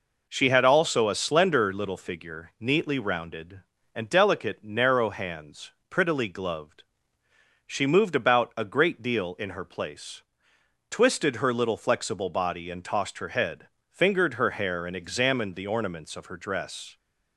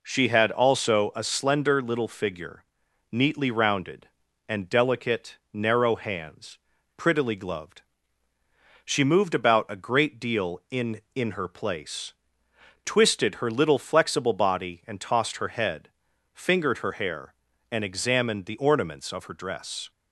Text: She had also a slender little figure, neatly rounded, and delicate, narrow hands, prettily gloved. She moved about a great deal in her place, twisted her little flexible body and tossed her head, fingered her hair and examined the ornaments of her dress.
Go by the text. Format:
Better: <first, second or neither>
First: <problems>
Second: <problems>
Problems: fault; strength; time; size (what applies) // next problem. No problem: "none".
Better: first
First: none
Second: says "in" twice; at 11.1 s